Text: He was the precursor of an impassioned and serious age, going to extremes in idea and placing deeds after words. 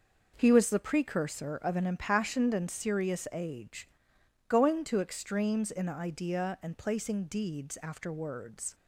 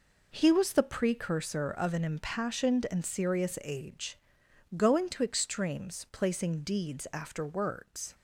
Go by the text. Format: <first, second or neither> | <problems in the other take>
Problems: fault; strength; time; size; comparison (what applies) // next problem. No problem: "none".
first | skips "in idea and"; at 6.0 s